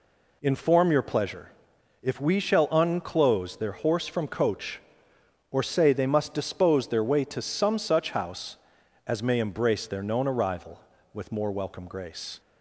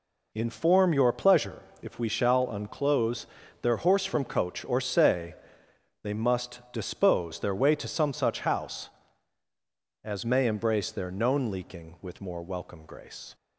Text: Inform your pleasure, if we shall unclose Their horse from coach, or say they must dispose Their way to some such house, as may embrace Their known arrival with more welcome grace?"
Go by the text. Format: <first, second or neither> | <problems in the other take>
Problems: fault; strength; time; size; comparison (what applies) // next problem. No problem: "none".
first | pauses between "unclose" and "Their"; slight; at 3.2 s; 0.34 s long // pauses between "say" and "they"; noticeable; at 5.3 s; 0.70 s long // says "leaking" for "arrival"; at 11.5 s